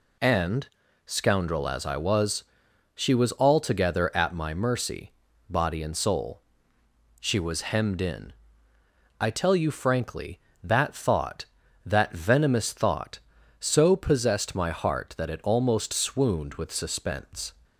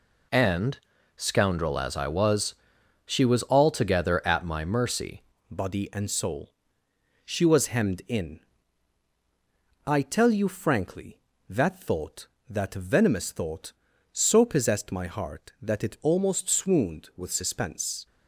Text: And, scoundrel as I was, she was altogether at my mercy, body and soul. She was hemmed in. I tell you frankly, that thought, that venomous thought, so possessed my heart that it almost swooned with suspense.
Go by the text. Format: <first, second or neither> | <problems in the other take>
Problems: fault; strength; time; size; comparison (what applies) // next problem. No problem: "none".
first | changes voice at "body"; from 5.4 s on; 12.6 s long